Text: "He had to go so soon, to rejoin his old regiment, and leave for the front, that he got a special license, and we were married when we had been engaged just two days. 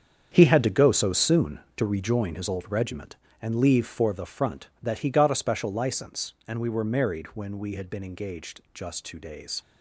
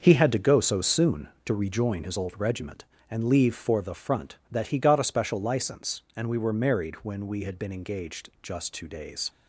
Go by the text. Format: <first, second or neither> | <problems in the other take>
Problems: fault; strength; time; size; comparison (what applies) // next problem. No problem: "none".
second | gets quieter; strong; throughout; 12 dB // starts louder than the rest; strong; until 1.3 s; 8 dB; also in the second